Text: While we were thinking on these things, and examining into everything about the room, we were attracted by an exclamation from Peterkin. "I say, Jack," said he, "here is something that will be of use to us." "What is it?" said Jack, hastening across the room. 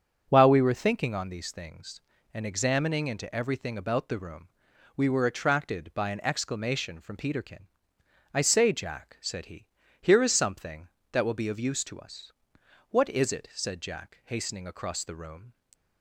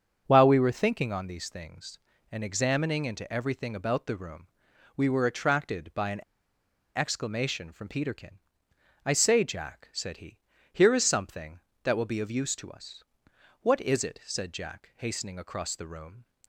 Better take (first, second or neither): first